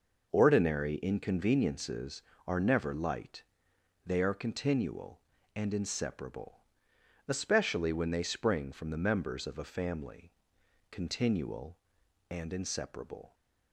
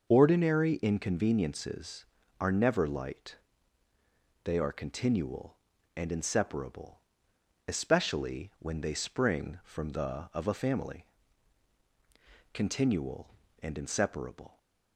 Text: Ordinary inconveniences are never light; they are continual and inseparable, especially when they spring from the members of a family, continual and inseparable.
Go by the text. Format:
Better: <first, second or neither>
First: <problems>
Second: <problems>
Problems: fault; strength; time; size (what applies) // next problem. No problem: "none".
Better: first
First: none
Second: skips "members"; at 10.3 s